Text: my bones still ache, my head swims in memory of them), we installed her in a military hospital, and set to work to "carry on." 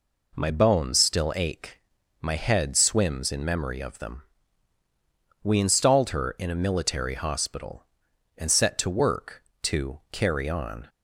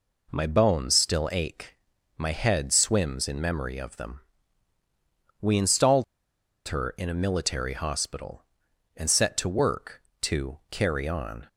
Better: first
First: none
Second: pauses between "installed" and "her"; noticeable; at 6.0 s; 0.64 s long

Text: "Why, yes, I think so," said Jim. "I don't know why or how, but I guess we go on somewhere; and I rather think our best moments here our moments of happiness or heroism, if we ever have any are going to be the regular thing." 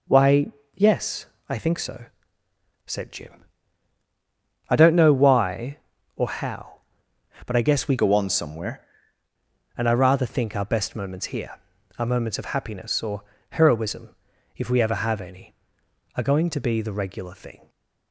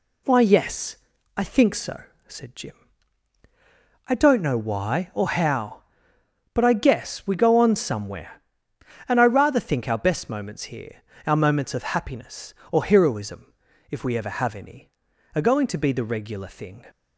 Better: second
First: changes voice from "go" to "somewhere"; from 7.9 to 8.8 s; 0.9 s long // pauses between "here" and "our"; at 11.5 s; 0.40 s long // pauses between "or" and "heroism"; slight; at 13.2 s; 0.30 s long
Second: pauses between "here" and "our"; slight; at 11.0 s; 0.24 s long

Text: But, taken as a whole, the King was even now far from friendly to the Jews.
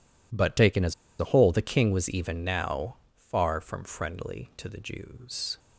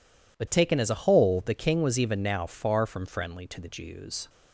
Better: second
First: pauses between "as" and "a"; slight; at 0.9 s; 0.26 s long // pauses between "now" and "far"; slight; at 2.9 s; 0.22 s long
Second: none

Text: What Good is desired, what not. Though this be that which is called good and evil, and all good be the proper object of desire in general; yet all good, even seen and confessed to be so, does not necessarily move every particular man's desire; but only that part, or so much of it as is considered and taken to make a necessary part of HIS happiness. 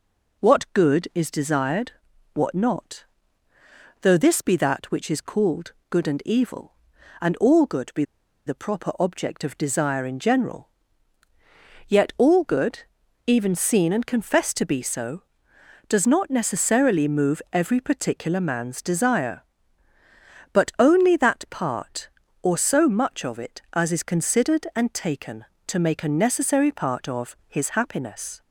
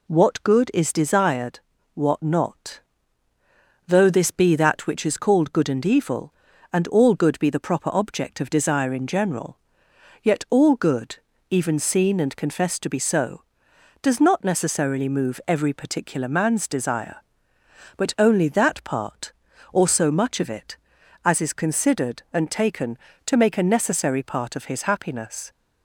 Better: second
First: pauses between "called" and "good"; slight; at 5.7 s; 0.18 s long // pauses between "be" and "the"; at 8.0 s; 0.42 s long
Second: none

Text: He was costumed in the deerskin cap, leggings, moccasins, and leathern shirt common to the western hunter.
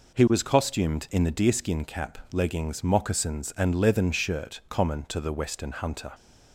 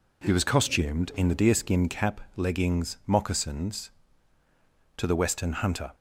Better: first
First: none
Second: skips "and leathern shirt common"; at 4.4 s

